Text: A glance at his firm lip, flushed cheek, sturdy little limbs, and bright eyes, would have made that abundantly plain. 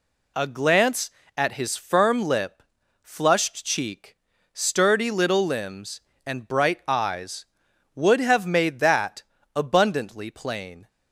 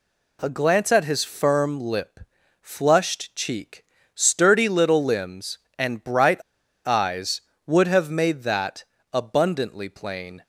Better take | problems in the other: first | pauses between "bright" and "eyes"; at 6.4 s; 0.42 s long // pauses between "that" and "abundantly"; slight; at 8.8 s; 0.30 s long; slight in the first

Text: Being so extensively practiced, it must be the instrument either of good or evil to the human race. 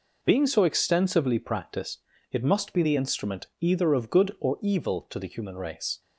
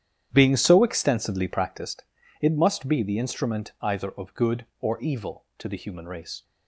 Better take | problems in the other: first | starts louder than the rest; strong; until 1.9 s; 10 dB

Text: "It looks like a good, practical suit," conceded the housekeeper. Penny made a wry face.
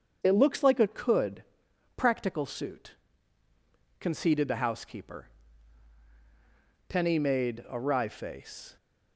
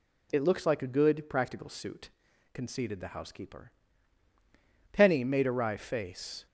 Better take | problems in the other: second | starts louder than the rest; until 1.2 s; 7 dB // says "could" for "good"; at 0.8 s

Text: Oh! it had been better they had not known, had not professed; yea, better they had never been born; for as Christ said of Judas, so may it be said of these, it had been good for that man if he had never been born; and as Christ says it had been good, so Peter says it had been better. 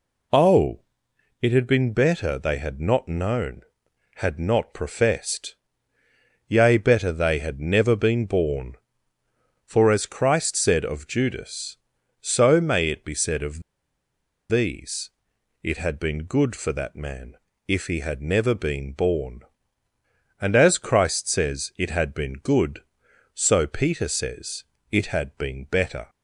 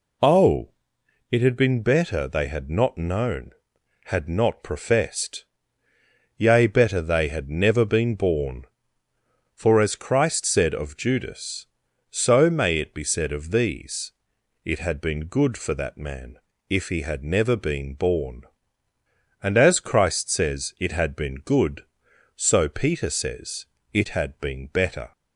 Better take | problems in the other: second | pauses between "of" and "these"; noticeable; at 13.6 s; 0.88 s long // pauses between "man" and "if"; slight; at 17.3 s; 0.30 s long; slight in the second // pauses between "says" and "it"; slight; at 24.6 s; 0.26 s long; slight in the second

